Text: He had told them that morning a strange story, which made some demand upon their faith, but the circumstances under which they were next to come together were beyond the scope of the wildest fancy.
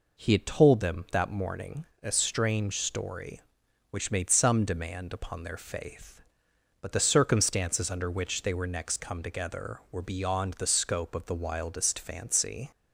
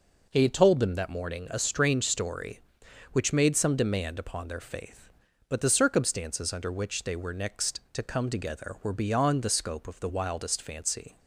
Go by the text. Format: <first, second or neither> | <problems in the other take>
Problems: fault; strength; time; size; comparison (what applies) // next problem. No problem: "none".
second | pauses between "morning" and "a"; slight; at 1.8 s; 0.16 s long // skips "to"; at 8.9 s